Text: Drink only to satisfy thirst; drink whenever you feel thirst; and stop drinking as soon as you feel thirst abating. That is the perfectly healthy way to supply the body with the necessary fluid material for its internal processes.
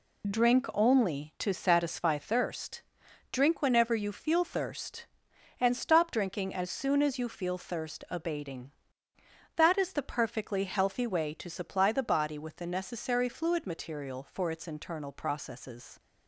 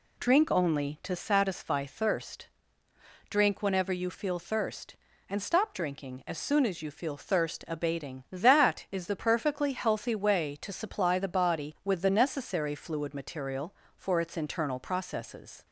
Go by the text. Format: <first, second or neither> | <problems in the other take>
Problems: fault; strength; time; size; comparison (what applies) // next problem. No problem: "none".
neither | none